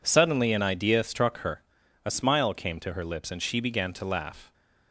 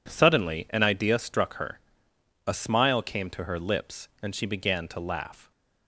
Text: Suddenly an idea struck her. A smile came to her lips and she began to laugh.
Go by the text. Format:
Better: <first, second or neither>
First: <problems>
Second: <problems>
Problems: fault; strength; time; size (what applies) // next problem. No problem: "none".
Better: neither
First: none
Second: none